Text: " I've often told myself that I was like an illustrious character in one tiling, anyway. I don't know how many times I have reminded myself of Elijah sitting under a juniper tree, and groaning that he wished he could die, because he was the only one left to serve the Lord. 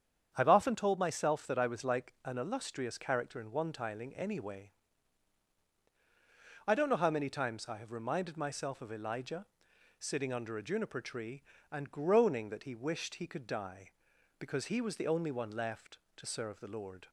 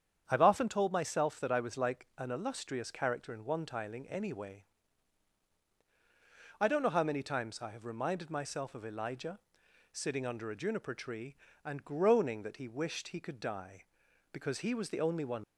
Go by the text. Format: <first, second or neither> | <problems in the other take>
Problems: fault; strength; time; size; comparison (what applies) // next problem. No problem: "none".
first | starts louder than the rest; strong; until 1.2 s; 8.5 dB; strong in the first // pauses between "Elijah" and "sitting"; noticeable; at 9.3 s; 0.54 s long; noticeable in the first // stops before "left to serve the Lord"; at 15.4 s